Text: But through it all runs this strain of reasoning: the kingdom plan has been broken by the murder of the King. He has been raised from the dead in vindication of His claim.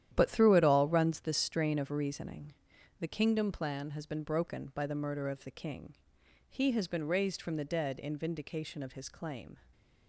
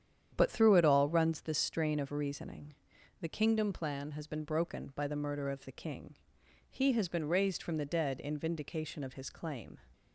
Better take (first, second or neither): second